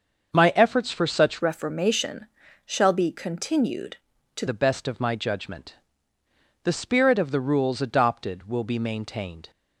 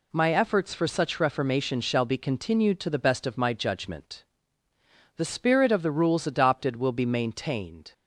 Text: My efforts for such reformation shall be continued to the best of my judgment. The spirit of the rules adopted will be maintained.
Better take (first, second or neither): second